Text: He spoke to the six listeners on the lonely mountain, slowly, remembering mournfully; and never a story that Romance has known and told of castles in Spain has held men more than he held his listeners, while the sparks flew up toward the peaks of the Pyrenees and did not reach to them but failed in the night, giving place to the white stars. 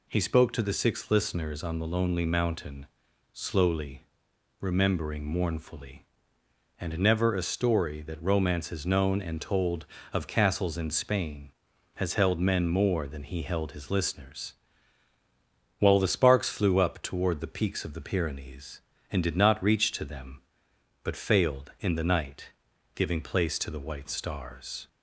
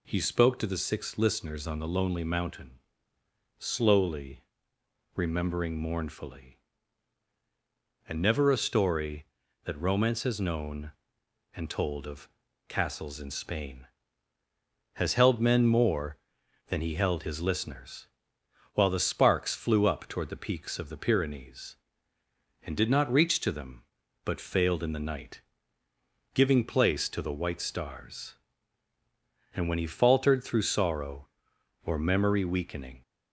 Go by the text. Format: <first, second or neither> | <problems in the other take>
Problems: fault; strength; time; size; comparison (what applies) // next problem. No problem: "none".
first | pauses between "of" and "castles"; at 12.2 s; 0.40 s long // goes on to say "And when he faltered through sorrow or memory weakening"; strong; from 29.5 s on; 3.4 s long